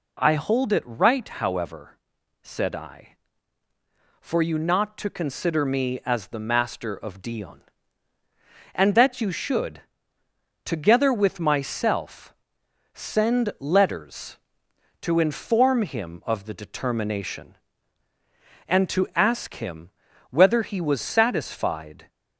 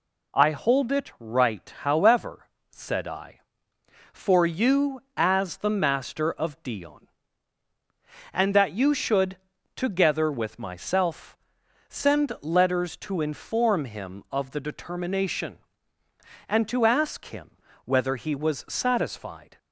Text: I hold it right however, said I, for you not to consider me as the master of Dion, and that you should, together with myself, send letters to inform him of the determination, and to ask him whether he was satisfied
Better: first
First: pauses between "him" and "whether"; at 19.9 s; 0.40 s long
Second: skips "not to consider me"; at 5.0 s // pauses between "him" and "whether"; slight; at 17.4 s; 0.36 s long

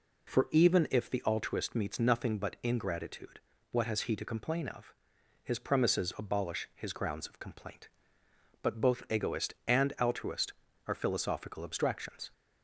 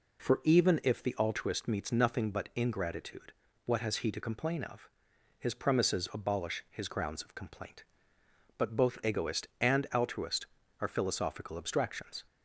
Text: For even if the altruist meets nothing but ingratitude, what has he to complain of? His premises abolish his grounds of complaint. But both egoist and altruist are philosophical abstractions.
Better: neither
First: none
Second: none

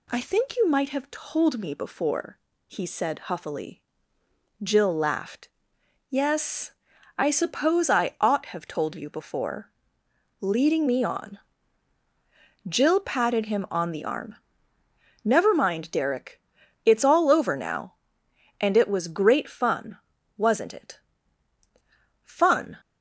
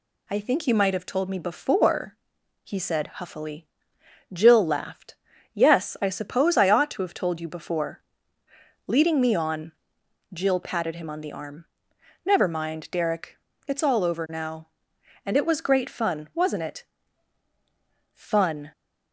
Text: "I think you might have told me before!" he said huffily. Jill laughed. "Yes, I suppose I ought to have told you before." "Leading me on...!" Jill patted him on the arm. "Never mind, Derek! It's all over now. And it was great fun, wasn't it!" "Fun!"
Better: second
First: skips "to"; at 8.4 s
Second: none

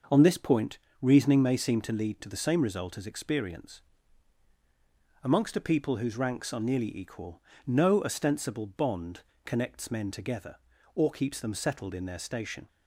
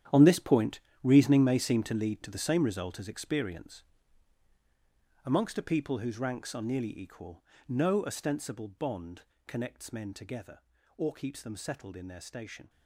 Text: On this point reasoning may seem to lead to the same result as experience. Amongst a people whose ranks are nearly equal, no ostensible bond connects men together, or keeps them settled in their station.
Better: first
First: starts louder than the rest; until 1.3 s; 6 dB // pauses between "point" and "reasoning"; slight; at 0.7 s; 0.22 s long // pauses between "bond" and "connects"; slight; at 9.2 s; 0.24 s long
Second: gets quieter; strong; throughout; 13.5 dB // starts louder than the rest; strong; until 1.3 s; 10 dB // pauses between "point" and "reasoning"; slight; at 0.8 s; 0.22 s long // pauses between "bond" and "connects"; slight; at 9.2 s; 0.24 s long

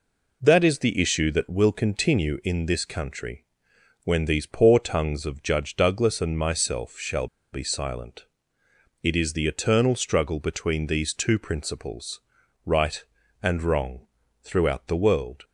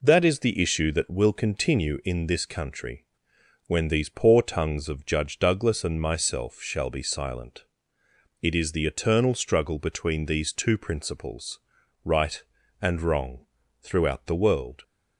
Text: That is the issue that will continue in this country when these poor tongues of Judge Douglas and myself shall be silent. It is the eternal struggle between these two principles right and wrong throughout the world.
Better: second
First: pauses between "country" and "when"; noticeable; at 3.4 s; 0.60 s long // pauses between "shall" and "be"; slight; at 7.2 s; 0.24 s long // pauses between "principles" and "right"; at 12.2 s; 0.42 s long // pauses between "wrong" and "throughout"; slight; at 14.0 s; 0.36 s long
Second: pauses between "country" and "when"; noticeable; at 3.0 s; 0.62 s long // pauses between "principles" and "right"; at 11.6 s; 0.42 s long // pauses between "wrong" and "throughout"; slight; at 13.4 s; 0.36 s long

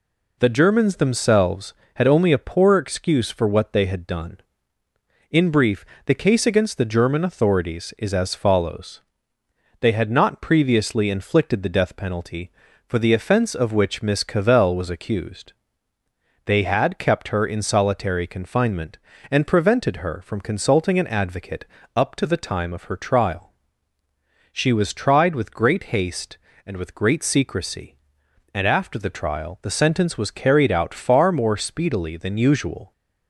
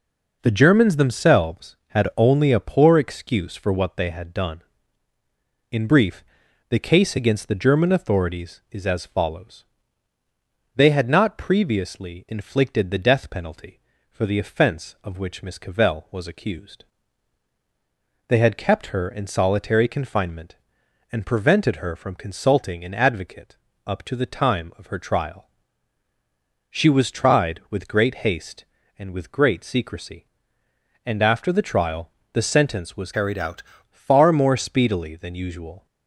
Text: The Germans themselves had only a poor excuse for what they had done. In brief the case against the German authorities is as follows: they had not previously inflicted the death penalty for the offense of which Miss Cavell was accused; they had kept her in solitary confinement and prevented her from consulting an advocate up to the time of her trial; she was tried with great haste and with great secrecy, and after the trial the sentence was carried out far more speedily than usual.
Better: first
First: pauses between "brief" and "the"; slight; at 5.8 s; 0.22 s long // pauses between "advocate" and "up"; slight; at 21.6 s; 0.30 s long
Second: pauses between "brief" and "the"; noticeable; at 6.2 s; 0.46 s long // pauses between "advocate" and "up"; slight; at 23.5 s; 0.28 s long // pauses between "trial" and "the"; slight; at 32.1 s; 0.22 s long // changes voice from "carried" to "out"; from 33.1 to 33.6 s; 0.5 s long

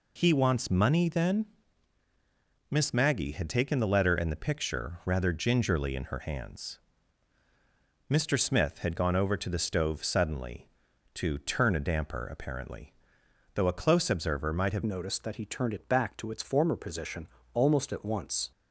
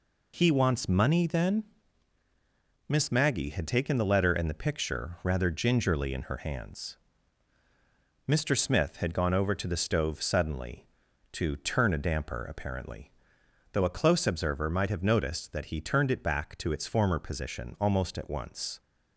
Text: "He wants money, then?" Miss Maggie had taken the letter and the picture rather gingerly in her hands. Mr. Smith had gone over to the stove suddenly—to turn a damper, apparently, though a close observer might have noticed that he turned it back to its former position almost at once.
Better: second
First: changes voice at "noticed"; from 14.8 s on; 3.7 s long // pauses between "position" and "almost"; slight; at 17.2 s; 0.28 s long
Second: none

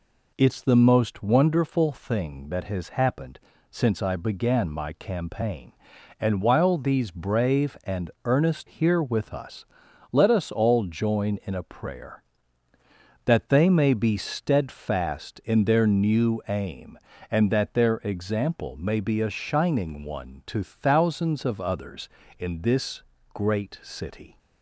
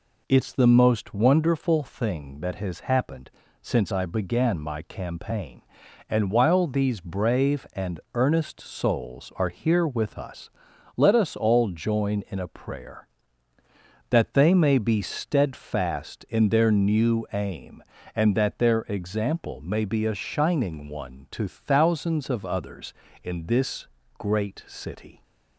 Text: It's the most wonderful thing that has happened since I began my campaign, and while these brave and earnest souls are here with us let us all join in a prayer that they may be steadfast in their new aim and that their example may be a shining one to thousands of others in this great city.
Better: second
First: pauses between "happened" and "since"; slight; at 3.3 s; 0.30 s long // pauses between "and" and "earnest"; slight; at 8.0 s; 0.16 s long // skips "souls are"; at 8.6 s // pauses between "us" and "let"; noticeable; at 9.6 s; 0.48 s long // pauses between "this" and "great"; slight; at 23.0 s; 0.32 s long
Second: pauses between "happened" and "since"; slight; at 3.3 s; 0.30 s long // pauses between "and" and "earnest"; slight; at 7.9 s; 0.16 s long // pauses between "us" and "let"; noticeable; at 10.4 s; 0.48 s long // pauses between "this" and "great"; slight; at 23.8 s; 0.32 s long

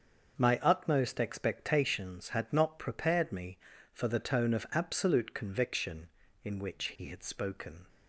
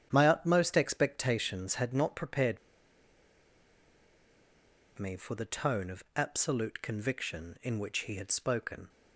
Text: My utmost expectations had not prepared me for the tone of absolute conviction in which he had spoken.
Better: first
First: starts louder than the rest; until 1.4 s; 6.5 dB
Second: starts louder than the rest; strong; until 1.1 s; 9 dB // pauses between "prepared" and "me"; strong; at 2.5 s; 2.3 s long

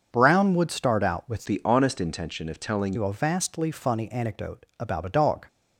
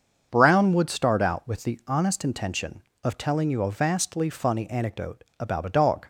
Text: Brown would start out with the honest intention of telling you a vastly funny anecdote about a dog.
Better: second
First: starts louder than the rest; until 1.1 s; 6.5 dB // changes voice from "the" to "telling"; from 1.4 to 2.9 s; 1.5 s long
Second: starts louder than the rest; until 1.3 s; 6.5 dB

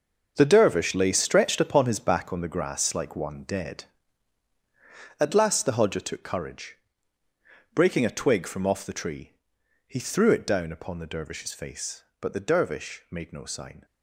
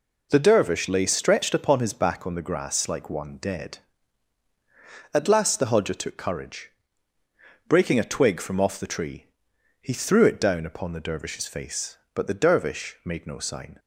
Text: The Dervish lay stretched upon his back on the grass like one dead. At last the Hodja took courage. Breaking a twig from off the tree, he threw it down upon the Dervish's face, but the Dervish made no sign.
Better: second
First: gets quieter; strong; throughout; 11 dB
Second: none

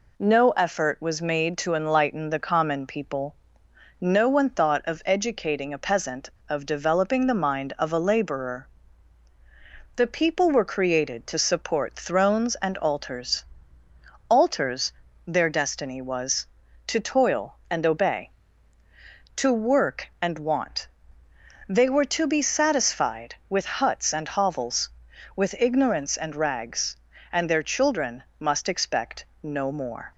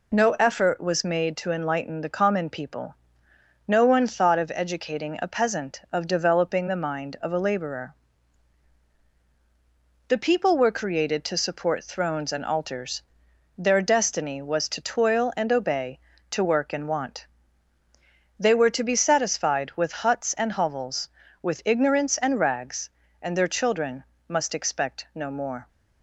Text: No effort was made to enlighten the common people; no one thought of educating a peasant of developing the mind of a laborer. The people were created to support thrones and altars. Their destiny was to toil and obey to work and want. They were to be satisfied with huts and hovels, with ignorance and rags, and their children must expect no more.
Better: second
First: says "altars" twice; at 14.2 s // pauses between "children" and "must"; slight; at 28.2 s; 0.16 s long // pauses between "expect" and "no"; slight; at 29.2 s; 0.18 s long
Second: pauses between "children" and "must"; slight; at 24.0 s; 0.26 s long

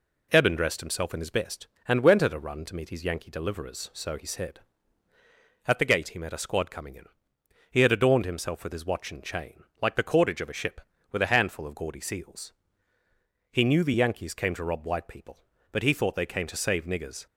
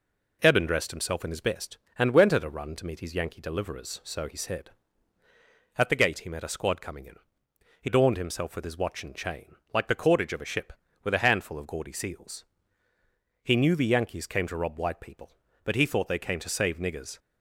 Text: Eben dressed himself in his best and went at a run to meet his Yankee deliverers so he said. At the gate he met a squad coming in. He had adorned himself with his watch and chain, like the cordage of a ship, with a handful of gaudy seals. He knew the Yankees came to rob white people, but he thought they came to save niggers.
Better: first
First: none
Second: skips "had"; at 7.8 s

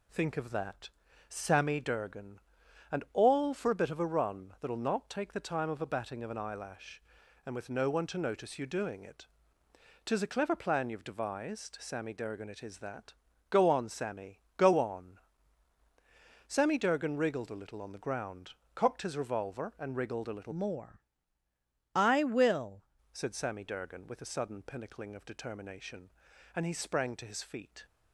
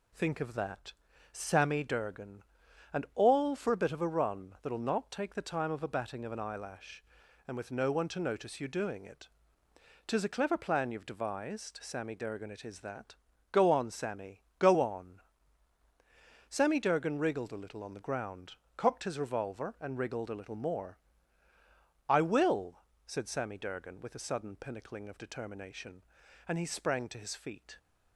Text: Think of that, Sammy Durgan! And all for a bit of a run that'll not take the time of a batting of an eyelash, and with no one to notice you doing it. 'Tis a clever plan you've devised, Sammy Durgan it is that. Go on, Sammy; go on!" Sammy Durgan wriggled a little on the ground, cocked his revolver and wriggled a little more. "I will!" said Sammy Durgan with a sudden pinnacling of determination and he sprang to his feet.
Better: second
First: changes voice from "more" to "will"; from 20.5 to 22.8 s; 2.3 s long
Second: none

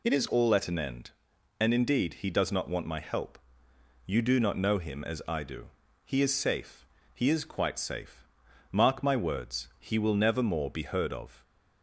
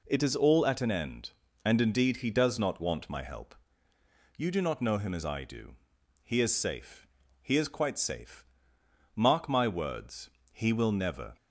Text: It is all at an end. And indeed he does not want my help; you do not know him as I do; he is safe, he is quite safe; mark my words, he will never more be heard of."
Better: first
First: none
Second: stops before "more be heard of"; at 11.3 s

